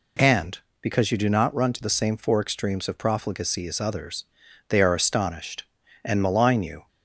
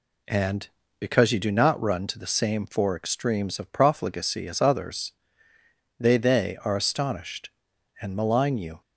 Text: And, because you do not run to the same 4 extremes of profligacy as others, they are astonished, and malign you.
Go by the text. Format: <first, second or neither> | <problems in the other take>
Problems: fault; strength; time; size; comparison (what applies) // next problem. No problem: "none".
first | says "they" twice; at 6.1 s